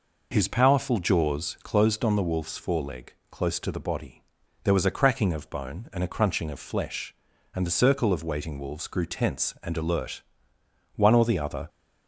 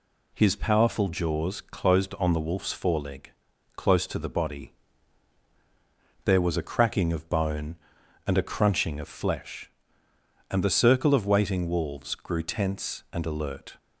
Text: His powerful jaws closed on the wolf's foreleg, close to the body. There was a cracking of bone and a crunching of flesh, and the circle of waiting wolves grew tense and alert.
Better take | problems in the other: second | goes on to say "One or the other"; noticeable; from 10.9 s on; 0.72 s long

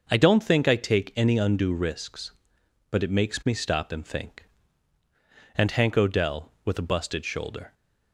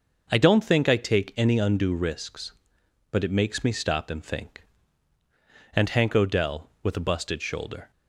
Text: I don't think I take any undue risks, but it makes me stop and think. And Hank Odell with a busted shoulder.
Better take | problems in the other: neither | starts louder than the rest; the same in both

